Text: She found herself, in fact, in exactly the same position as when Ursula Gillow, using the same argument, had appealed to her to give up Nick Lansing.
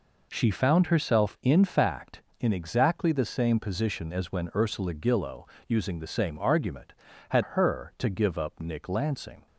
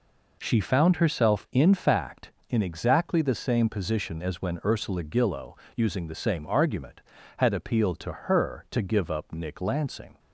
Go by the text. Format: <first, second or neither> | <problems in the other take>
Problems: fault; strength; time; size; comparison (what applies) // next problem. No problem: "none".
second | skips "appealed to"; at 7.4 s